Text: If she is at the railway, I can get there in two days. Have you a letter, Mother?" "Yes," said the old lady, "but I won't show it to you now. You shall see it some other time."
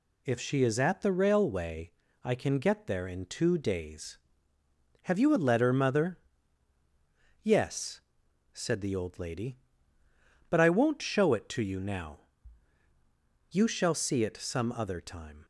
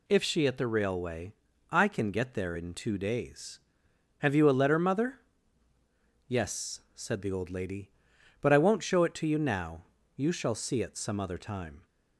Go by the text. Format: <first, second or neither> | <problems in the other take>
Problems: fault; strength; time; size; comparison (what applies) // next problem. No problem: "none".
first | skips "is"; at 0.4 s